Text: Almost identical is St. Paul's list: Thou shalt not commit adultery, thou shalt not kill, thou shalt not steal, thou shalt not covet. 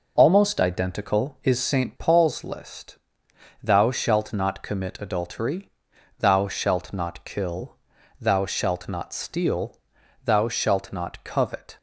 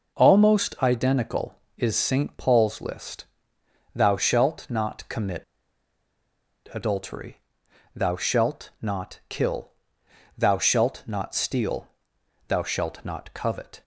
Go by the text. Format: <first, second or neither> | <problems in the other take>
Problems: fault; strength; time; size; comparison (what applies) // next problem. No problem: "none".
first | pauses between "commit" and "adultery"; strong; at 5.4 s; 1.2 s long